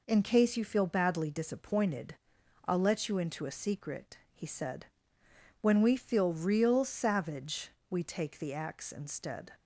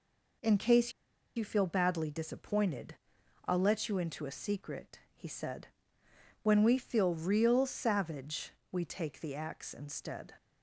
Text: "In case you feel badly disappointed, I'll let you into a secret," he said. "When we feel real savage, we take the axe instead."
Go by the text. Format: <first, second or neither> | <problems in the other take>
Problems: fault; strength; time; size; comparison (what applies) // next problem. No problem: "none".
first | pauses between "case" and "you"; at 0.9 s; 0.45 s long